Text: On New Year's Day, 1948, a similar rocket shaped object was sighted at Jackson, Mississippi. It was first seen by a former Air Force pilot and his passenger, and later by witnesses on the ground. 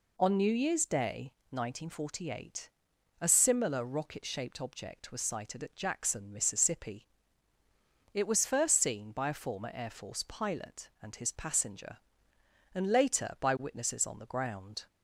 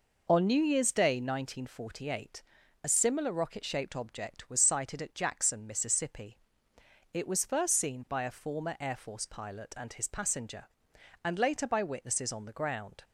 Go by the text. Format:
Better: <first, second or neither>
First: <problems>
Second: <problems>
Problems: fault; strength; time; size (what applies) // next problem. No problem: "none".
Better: neither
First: none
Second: none